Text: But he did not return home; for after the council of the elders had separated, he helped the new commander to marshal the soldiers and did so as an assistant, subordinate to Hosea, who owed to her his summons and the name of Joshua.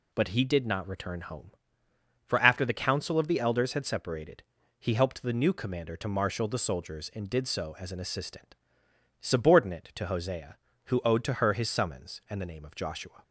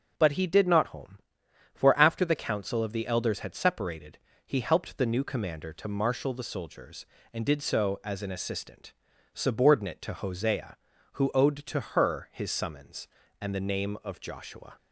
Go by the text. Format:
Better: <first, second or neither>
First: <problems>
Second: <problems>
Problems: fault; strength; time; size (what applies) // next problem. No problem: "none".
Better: first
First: none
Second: skips "return"; at 0.8 s